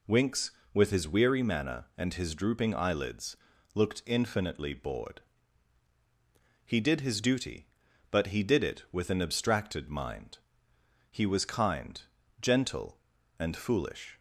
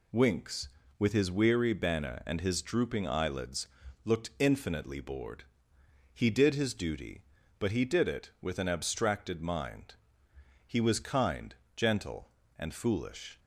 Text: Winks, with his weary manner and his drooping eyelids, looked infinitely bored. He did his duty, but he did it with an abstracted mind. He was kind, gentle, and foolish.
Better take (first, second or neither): first